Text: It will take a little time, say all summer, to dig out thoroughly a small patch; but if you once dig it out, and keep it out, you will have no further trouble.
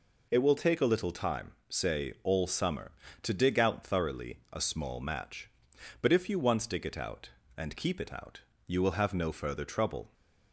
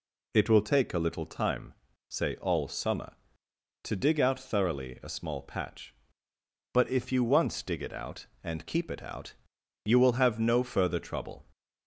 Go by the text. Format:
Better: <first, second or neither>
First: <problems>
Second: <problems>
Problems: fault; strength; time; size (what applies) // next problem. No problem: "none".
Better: second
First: says "match" for "patch"; at 5.0 s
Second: none